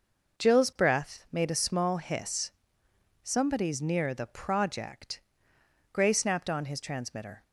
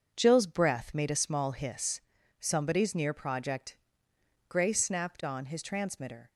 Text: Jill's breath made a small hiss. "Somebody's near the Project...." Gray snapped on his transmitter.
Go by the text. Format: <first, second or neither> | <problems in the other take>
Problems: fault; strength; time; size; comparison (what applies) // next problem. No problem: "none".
first | starts louder than the rest; until 1.1 s; 6.5 dB // skips "the"; at 3.1 s